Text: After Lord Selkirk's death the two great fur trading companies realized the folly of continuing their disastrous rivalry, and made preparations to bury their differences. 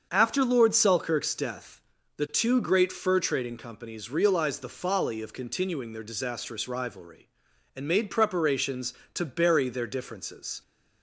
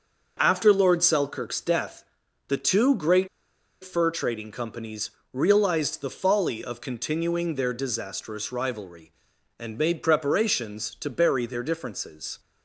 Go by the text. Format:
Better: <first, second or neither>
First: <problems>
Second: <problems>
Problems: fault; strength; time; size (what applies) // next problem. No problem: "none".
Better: first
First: starts louder than the rest; until 1.1 s; 7 dB // pauses between "death" and "the"; slight; at 1.8 s; 0.34 s long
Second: starts louder than the rest; until 1.4 s; 6.5 dB // pauses between "death" and "the"; at 2.0 s; 0.42 s long // pauses between "great" and "fur"; noticeable; at 3.2 s; 0.55 s long // pauses between "companies" and "realized"; slight; at 5.0 s; 0.22 s long